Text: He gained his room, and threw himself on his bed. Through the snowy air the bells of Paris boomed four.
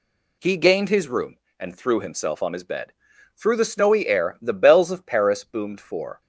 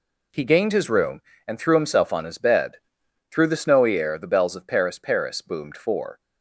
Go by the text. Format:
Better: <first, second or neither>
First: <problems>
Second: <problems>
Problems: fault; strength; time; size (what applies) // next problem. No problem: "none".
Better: first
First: none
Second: says "Paris" twice; at 4.9 s